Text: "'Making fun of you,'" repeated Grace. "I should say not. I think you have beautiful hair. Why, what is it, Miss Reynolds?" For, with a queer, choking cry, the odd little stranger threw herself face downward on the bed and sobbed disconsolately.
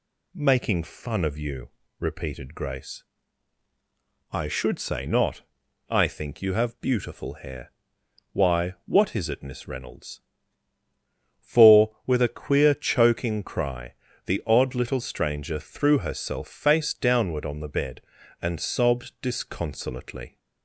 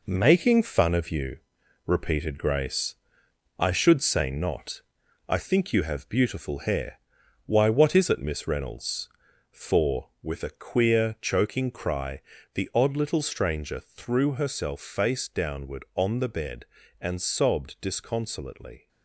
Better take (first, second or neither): first